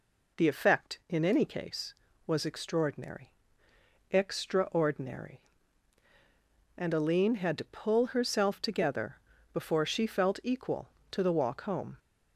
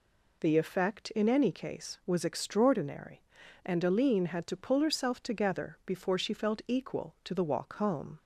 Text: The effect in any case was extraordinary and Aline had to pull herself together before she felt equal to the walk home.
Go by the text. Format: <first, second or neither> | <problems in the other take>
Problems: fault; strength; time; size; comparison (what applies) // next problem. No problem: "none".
second | says "extraordinary" twice; at 4.0 s // pauses between "together" and "before"; slight; at 9.1 s; 0.34 s long